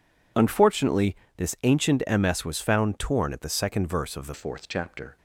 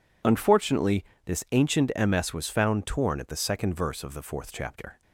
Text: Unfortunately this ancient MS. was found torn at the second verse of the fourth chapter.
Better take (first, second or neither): second